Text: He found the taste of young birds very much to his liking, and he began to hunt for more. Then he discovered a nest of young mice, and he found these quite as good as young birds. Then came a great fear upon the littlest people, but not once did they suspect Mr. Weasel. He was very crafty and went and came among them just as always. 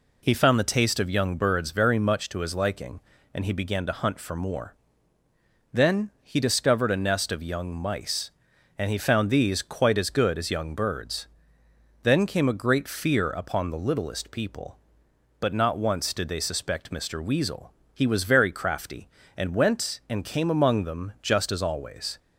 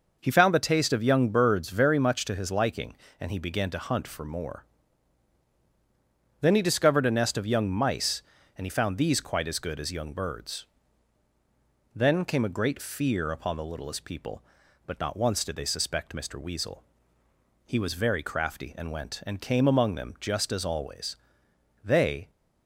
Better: first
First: none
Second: goes on to say "They"; slight; from 21.8 s on; 0.48 s long

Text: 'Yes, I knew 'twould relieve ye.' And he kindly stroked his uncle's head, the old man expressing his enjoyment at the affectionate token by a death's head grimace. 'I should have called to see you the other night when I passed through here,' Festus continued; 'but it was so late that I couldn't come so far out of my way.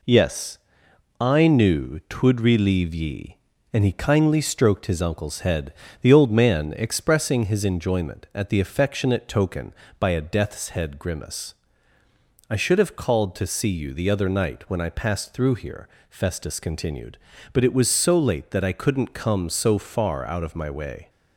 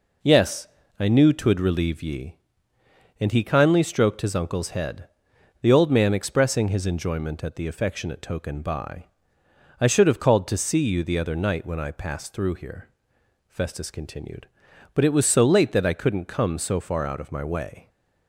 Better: first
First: none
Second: skips "a death's head grimace"; at 9.4 s

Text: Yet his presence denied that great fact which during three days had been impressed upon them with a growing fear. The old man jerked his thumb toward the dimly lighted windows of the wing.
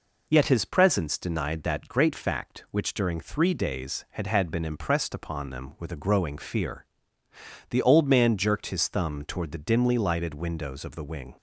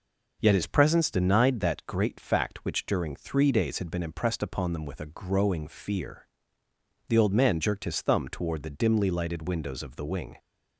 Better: second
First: says "had" twice; at 4.2 s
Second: none

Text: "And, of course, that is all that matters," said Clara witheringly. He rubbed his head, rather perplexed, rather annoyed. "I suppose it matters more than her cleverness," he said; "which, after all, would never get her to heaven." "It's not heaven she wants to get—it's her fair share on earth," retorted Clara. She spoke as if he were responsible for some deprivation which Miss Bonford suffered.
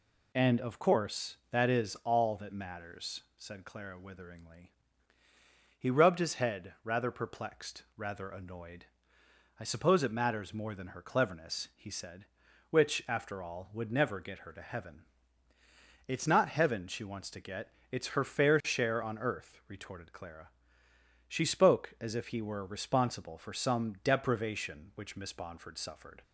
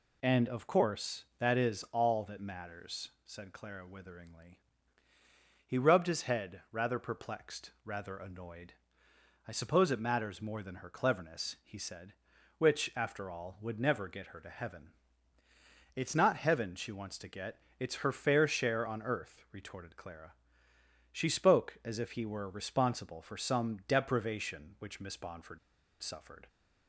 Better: first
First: none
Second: pauses between "Bonford" and "suffered"; at 25.5 s; 0.44 s long

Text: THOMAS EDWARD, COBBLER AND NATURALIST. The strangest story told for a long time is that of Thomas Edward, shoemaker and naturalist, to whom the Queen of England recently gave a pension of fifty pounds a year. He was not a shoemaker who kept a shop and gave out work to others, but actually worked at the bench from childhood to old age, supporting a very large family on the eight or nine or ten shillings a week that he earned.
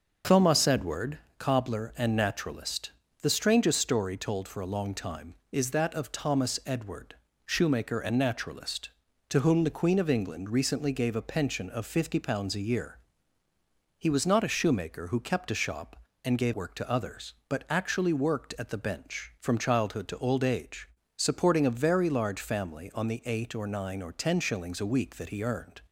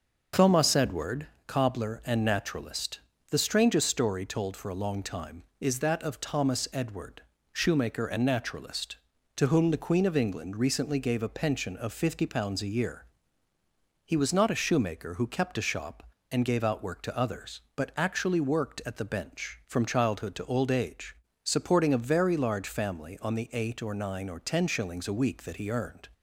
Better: second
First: starts louder than the rest; until 1.4 s; 6 dB // skips "out"; at 16.5 s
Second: starts louder than the rest; until 1.5 s; 6 dB

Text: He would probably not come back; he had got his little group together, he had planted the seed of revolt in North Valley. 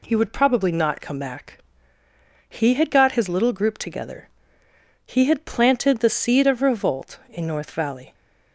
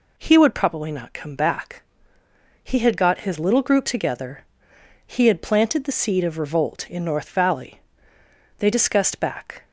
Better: first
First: none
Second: goes on to say "They discussed back"; noticeable; from 8.5 s on; 1.0 s long

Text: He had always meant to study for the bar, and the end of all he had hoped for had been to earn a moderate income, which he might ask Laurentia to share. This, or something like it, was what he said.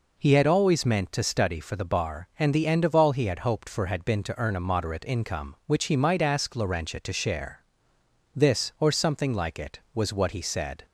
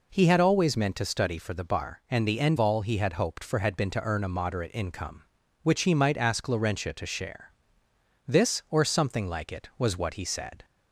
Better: first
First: none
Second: skips "of"; at 2.5 s

